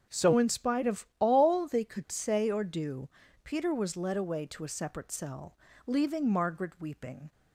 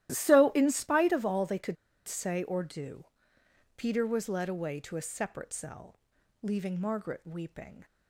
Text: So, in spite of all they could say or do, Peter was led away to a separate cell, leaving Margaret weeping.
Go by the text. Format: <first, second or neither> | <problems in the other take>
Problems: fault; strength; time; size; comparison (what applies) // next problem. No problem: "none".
first | starts louder than the rest; strong; until 1.1 s; 13.5 dB; also in the first // pauses between "could" and "say"; slight; at 1.7 s; 0.33 s long